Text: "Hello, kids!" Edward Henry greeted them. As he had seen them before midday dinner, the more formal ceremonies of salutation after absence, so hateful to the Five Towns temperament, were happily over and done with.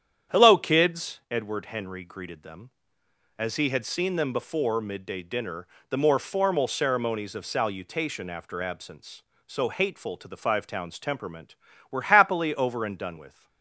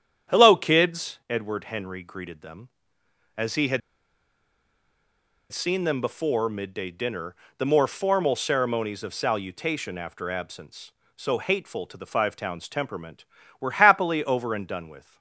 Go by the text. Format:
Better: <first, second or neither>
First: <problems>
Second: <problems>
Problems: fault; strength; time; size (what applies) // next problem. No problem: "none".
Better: first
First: starts louder than the rest; strong; until 1.4 s; 9 dB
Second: starts louder than the rest; strong; until 1.4 s; 9 dB // pauses between "had" and "seen"; strong; at 3.8 s; 1.7 s long